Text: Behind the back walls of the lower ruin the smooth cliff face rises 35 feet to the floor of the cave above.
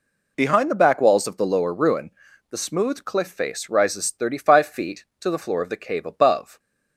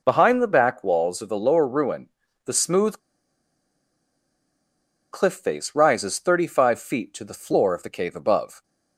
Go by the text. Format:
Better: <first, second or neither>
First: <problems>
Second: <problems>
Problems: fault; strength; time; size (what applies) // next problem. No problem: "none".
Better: first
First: pauses between "ruin" and "the"; at 2.0 s; 0.40 s long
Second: pauses between "ruin" and "the"; slight; at 2.0 s; 0.36 s long // pauses between "smooth" and "cliff"; strong; at 2.9 s; 2.1 s long